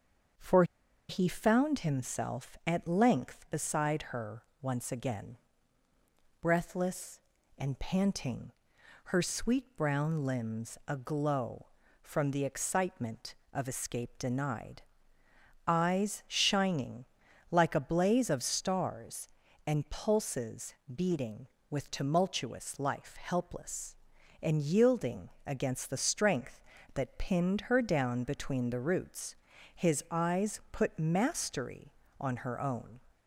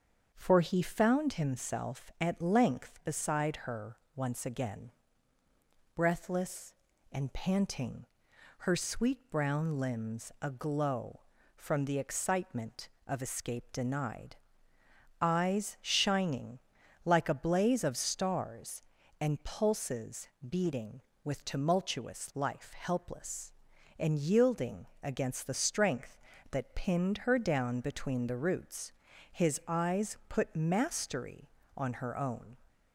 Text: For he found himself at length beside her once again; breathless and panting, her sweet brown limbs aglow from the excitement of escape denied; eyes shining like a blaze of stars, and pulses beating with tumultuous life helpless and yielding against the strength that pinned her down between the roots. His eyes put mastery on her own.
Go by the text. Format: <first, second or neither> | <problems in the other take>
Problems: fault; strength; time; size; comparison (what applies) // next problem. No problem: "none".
second | starts louder than the rest; strong; until 1.8 s; 7 dB; strong in the second // pauses between "For" and "he"; at 0.6 s; 0.45 s long // pauses between "her" and "once"; slight; at 4.4 s; 0.18 s long; slight in the second // pauses between "shining" and "like"; noticeable; at 17.0 s; 0.46 s long; noticeable in the second // pauses between "pulses" and "beating"; slight; at 20.7 s; 0.20 s long; slight in the second // pauses between "yielding" and "against"; slight; at 25.2 s; 0.16 s long; slight in the second